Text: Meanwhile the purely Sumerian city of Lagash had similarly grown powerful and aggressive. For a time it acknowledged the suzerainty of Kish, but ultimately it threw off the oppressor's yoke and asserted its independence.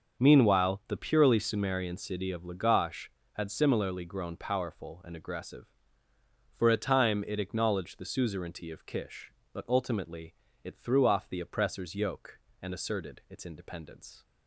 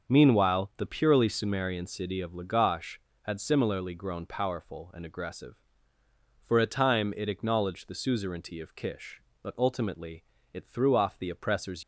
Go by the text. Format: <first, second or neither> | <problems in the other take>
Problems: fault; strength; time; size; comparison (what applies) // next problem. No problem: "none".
first | starts louder than the rest; until 1.1 s; 6.5 dB; also in the first // pauses between "ultimately" and "it"; slight; at 10.2 s; 0.30 s long; slight in the first // stops before "yoke and asserted its independence"; at 11.8 s